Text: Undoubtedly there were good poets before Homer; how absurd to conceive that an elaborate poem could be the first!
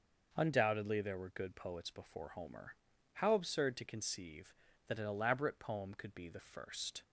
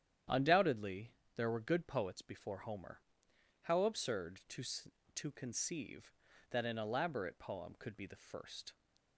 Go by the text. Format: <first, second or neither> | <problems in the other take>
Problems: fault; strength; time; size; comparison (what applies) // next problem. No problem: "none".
first | starts louder than the rest; strong; until 1.5 s; 9.5 dB // pauses between "Undoubtedly" and "there"; slight; at 1.1 s; 0.25 s long // says "to" twice; at 5.1 s